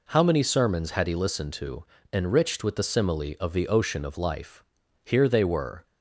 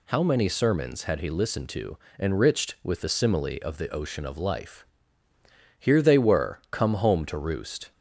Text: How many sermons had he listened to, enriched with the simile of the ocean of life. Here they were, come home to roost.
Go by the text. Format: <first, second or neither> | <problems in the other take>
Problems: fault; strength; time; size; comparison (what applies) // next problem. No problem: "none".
second | stops before "come home to roost"; at 5.8 s